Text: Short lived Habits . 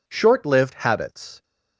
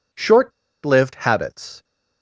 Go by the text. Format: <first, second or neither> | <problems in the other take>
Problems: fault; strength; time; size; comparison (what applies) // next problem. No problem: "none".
first | pauses between "Short" and "lived"; slight; at 0.5 s; 0.32 s long